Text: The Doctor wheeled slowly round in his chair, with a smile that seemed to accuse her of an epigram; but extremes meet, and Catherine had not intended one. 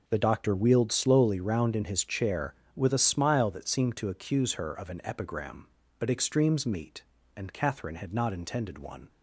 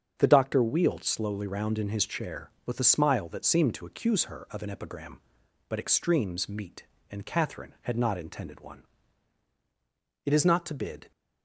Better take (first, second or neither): first